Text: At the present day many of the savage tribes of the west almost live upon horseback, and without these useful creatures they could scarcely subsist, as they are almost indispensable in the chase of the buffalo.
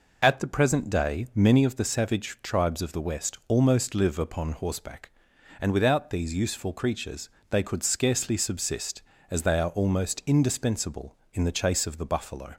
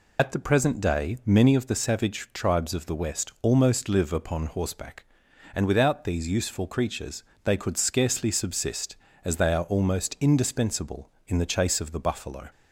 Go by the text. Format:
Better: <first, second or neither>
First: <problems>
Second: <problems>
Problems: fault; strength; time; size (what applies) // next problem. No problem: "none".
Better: first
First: pauses between "creatures" and "they"; slight; at 7.3 s; 0.18 s long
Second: loses the start of "At"; at 0.1 s; 50 ms // pauses between "creatures" and "they"; slight; at 7.2 s; 0.18 s long